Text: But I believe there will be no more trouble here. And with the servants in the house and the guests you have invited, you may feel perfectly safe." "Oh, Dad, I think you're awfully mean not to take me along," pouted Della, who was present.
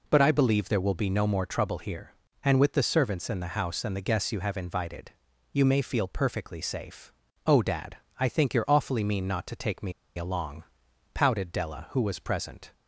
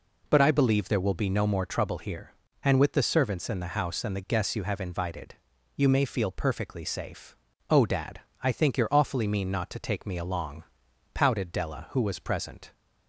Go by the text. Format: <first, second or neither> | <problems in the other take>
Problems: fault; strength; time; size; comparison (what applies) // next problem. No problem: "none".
second | pauses between "me" and "along"; slight; at 9.9 s; 0.26 s long